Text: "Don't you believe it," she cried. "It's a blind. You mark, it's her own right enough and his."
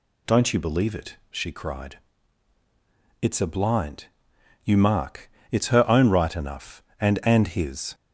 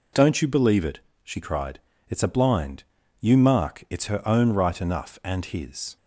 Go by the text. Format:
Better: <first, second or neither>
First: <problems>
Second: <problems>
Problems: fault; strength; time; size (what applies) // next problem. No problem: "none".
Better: second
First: says "and" twice; at 7.2 s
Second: none